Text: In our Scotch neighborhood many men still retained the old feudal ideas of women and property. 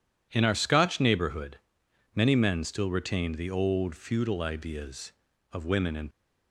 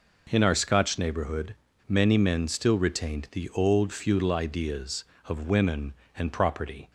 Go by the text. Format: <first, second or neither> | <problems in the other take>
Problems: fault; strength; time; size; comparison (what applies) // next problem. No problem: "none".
second | pauses between "neighborhood" and "many"; noticeable; at 1.5 s; 0.58 s long; slight in the second // stops before "property"; at 6.1 s